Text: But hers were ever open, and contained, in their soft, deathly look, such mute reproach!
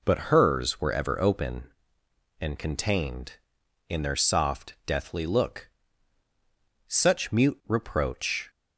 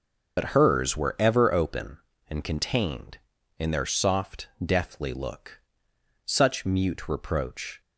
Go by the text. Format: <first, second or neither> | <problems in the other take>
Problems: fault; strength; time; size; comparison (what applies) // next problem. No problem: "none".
first | loses the start of "But"; at 0.3 s; 55 ms